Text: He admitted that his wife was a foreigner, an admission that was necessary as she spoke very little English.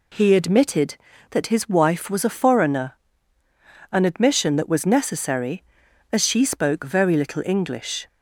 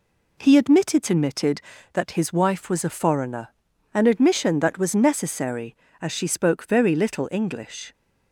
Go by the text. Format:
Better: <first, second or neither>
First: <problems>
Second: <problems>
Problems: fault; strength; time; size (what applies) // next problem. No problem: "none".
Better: first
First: none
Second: says "admitted" twice; at 1.1 s